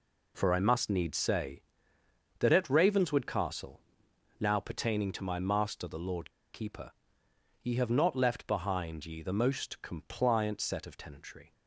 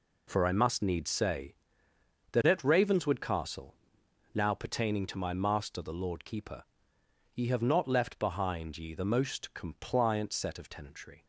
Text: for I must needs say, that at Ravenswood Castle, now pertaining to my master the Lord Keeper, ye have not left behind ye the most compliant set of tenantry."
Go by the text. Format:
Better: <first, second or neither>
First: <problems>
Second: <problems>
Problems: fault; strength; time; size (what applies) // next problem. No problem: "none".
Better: second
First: pauses between "Lord" and "Keeper"; slight; at 6.2 s; 0.23 s long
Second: none